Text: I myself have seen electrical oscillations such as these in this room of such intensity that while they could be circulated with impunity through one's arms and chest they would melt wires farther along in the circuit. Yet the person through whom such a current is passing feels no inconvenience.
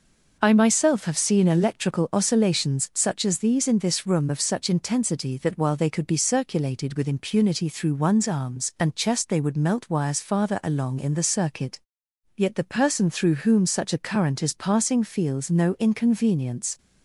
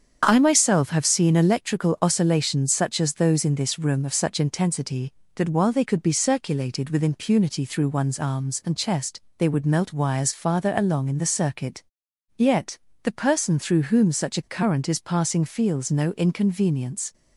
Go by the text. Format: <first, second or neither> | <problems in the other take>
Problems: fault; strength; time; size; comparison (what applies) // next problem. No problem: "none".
first | starts louder than the rest; strong; until 1.2 s; 7.5 dB // says "those" for "these"; at 3.1 s // pauses between "chest" and "they"; slight; at 9.1 s; 0.16 s long // pauses between "Yet" and "the"; slight; at 12.7 s; 0.24 s long